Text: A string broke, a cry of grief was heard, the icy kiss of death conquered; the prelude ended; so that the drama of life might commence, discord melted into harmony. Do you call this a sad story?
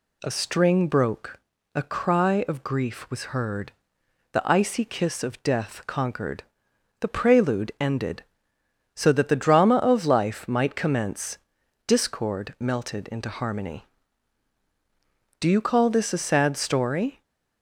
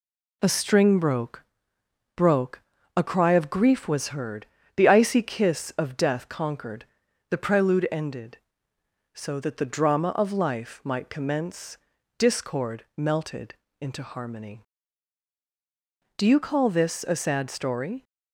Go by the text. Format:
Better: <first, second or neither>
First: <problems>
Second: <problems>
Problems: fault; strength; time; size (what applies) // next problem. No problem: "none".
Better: first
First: none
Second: says "broke" twice; at 2.1 s // pauses between "melted" and "into"; slight; at 13.5 s; 0.26 s long